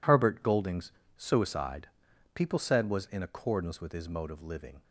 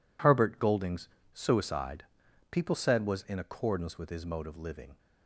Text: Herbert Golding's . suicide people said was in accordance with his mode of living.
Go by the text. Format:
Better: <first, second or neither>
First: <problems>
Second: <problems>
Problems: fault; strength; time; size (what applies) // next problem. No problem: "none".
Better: neither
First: pauses between "suicide" and "people"; noticeable; at 1.8 s; 0.46 s long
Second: pauses between "suicide" and "people"; noticeable; at 2.0 s; 0.46 s long